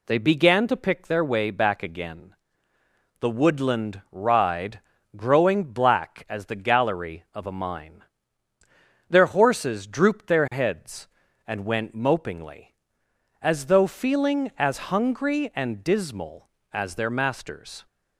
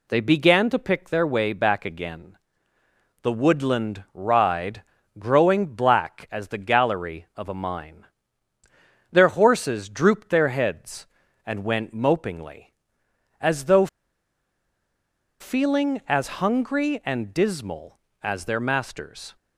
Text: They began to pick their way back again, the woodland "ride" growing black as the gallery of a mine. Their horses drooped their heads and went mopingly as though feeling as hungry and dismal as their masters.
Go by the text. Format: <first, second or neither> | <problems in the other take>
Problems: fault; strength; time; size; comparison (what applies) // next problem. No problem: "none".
first | pauses between "ride" and "growing"; slight; at 4.8 s; 0.36 s long; slight in the first // pauses between "though" and "feeling"; strong; at 13.8 s; 1.5 s long